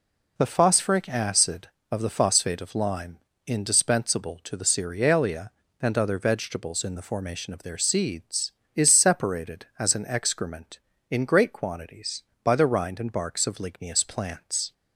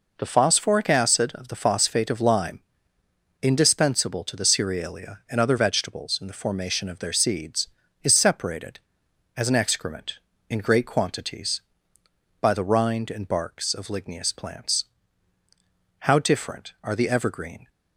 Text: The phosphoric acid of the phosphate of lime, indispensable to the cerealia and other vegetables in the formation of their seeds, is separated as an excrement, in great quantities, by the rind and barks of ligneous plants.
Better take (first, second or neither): first